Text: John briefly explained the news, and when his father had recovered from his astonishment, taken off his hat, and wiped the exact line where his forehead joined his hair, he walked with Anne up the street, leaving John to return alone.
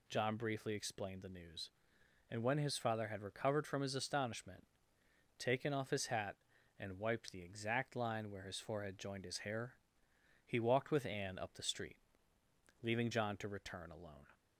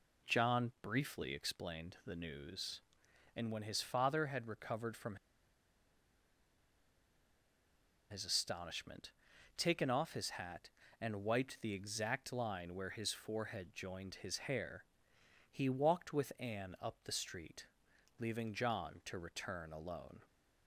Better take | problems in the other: first | pauses between "from" and "his"; strong; at 5.1 s; 2.9 s long

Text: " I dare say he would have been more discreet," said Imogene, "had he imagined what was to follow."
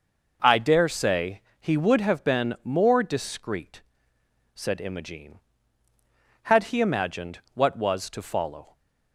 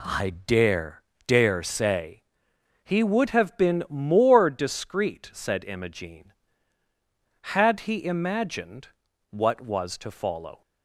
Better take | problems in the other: first | says "dare" twice; at 1.2 s // pauses between "say" and "he"; noticeable; at 2.2 s; 0.60 s long; slight in the first // pauses between "imagined" and "what"; at 8.8 s; 0.42 s long

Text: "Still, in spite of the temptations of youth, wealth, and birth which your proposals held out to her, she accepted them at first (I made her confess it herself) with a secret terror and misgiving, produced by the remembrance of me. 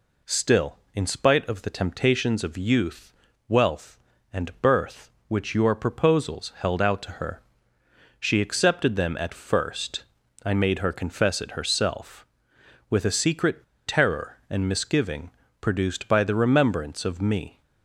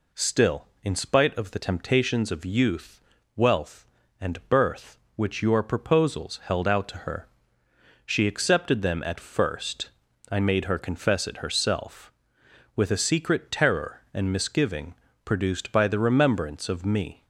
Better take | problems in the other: second | pauses between "secret" and "terror"; slight; at 13.6 s; 0.22 s long

